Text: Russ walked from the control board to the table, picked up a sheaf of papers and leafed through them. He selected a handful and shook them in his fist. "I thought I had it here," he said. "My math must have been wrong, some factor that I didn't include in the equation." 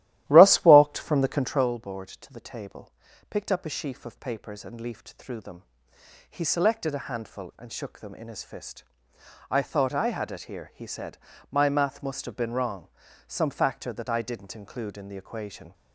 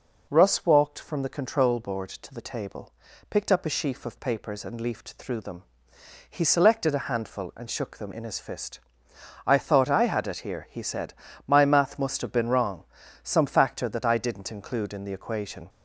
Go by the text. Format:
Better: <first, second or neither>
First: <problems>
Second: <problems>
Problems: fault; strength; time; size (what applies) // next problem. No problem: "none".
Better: second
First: starts louder than the rest; strong; until 1.7 s; 14 dB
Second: none